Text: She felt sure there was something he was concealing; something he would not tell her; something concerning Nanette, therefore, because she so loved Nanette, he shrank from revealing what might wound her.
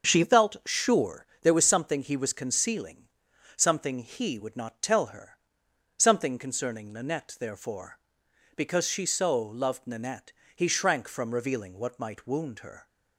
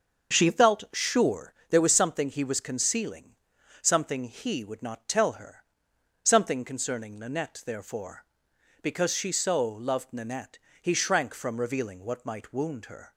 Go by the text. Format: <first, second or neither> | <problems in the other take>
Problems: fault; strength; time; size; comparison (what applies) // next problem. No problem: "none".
neither | starts louder than the rest; the same in both // pauses between "sure" and "there"; slight; the same in both